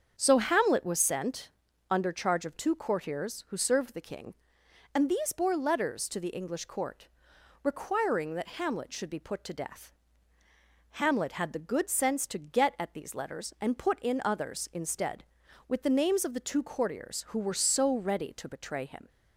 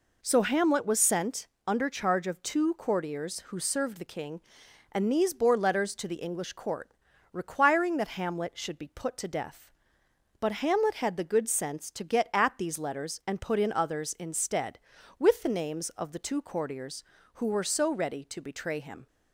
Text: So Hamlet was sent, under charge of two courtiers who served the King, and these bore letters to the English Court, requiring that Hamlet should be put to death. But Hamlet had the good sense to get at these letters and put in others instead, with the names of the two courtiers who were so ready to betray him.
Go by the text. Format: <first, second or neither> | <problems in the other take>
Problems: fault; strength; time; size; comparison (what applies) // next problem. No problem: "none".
second | starts louder than the rest; strong; until 1.1 s; 7 dB // skips "But"; at 10.4 s